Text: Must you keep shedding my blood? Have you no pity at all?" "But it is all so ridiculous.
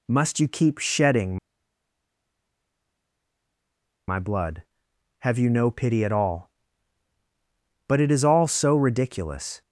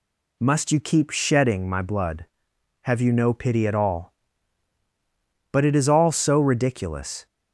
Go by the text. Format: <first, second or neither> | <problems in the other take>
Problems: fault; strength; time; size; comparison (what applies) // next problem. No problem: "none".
second | pauses between "shedding" and "my"; strong; at 1.3 s; 2.7 s long